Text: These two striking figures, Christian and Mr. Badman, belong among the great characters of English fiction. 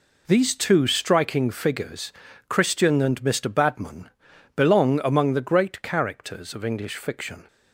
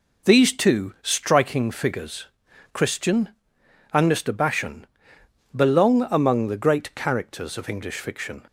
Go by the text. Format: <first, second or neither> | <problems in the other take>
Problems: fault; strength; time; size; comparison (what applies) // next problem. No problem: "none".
first | says "Bashan" for "Badman"; at 4.3 s